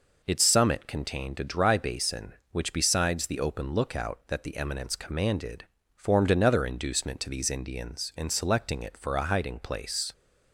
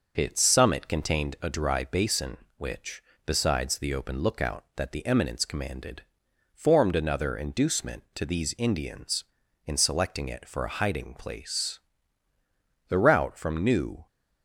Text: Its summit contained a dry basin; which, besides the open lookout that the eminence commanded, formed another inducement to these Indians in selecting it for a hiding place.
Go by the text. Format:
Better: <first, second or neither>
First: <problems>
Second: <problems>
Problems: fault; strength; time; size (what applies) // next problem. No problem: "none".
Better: first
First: none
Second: goes on to say "The route from New"; noticeable; from 12.8 s on; 1.1 s long